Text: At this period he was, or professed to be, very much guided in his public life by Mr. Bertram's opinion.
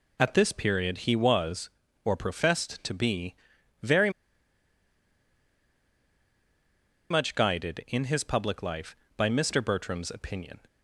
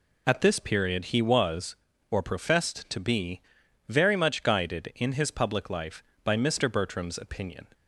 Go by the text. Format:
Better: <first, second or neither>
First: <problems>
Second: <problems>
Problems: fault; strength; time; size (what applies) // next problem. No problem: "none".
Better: second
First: pauses between "very" and "much"; strong; at 4.0 s; 3.0 s long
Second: none